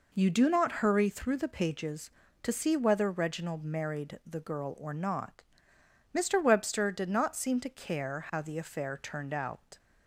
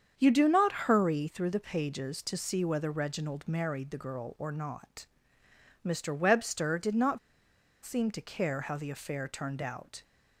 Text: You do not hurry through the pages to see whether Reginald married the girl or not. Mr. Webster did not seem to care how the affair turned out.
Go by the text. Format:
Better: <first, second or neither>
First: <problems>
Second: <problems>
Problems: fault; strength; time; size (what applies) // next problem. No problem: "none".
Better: first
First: none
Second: starts louder than the rest; strong; until 1.1 s; 7.5 dB // pauses between "not" and "seem"; noticeable; at 7.1 s; 0.66 s long